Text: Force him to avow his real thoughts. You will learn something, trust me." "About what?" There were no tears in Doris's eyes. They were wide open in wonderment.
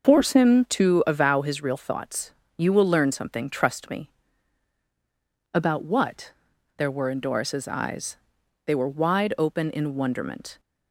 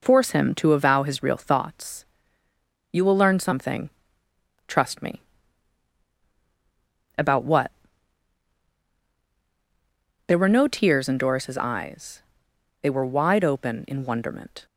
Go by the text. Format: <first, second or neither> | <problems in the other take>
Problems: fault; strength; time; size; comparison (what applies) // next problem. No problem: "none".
second | starts louder than the rest; noticeable; until 1.1 s; 6 dB // skips "no tears"; at 7.0 s